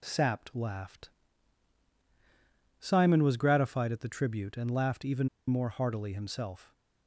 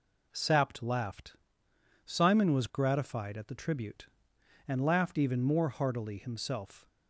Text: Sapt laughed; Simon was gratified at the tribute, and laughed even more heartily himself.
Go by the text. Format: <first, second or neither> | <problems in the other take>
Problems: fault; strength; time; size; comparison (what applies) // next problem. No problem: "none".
second | pauses between "even" and "more"; slight; at 5.2 s; 0.20 s long